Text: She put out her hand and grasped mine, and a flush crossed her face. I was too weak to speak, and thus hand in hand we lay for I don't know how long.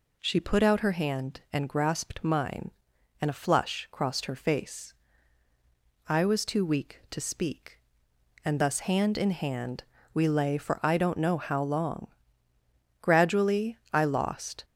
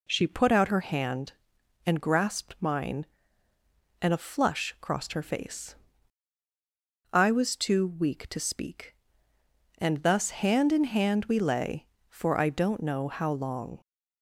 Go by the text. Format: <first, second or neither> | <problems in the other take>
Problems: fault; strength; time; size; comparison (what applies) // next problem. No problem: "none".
second | pauses between "hand" and "we"; slight; at 9.8 s; 0.28 s long // goes on to say "Gradually I lost"; from 13.0 s on; 1.6 s long